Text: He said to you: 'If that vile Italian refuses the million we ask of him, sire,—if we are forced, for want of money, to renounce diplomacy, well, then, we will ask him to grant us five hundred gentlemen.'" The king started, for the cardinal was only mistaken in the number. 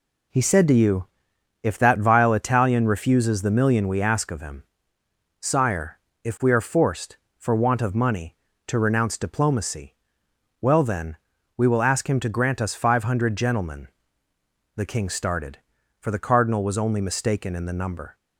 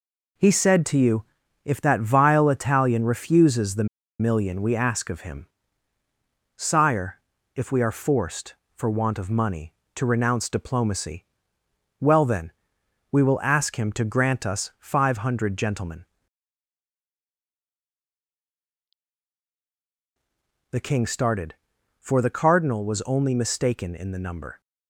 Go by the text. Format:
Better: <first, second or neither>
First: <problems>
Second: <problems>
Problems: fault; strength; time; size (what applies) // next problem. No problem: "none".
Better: first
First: none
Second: pauses between "the" and "million"; slight; at 3.8 s; 0.34 s long